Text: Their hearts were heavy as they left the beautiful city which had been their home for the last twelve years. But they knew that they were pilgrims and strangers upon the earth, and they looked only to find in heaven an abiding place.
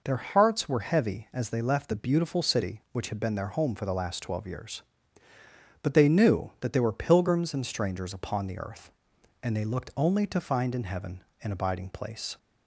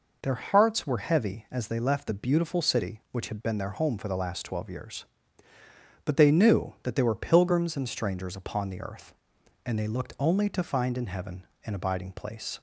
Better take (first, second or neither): neither